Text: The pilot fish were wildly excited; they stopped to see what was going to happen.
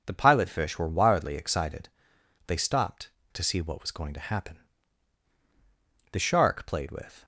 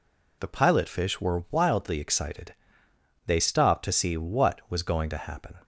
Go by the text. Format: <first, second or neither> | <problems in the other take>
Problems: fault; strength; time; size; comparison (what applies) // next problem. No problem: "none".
second | goes on to say "The shark played with"; noticeable; from 6.1 s on; 1.1 s long